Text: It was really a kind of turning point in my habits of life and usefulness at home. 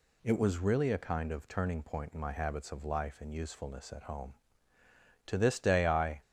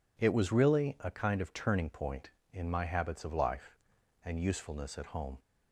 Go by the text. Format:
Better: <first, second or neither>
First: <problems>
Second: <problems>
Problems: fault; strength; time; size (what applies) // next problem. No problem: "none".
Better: second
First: goes on to say "To this day I"; noticeable; from 5.2 s on; 0.94 s long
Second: none